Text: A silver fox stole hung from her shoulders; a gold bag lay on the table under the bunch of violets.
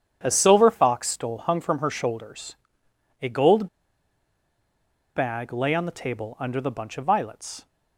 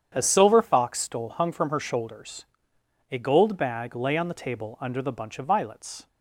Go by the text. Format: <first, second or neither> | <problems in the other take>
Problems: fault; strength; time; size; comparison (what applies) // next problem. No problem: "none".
second | starts louder than the rest; strong; until 1.2 s; 8.5 dB; strong in the second // pauses between "gold" and "bag"; strong; at 3.6 s; 1.4 s long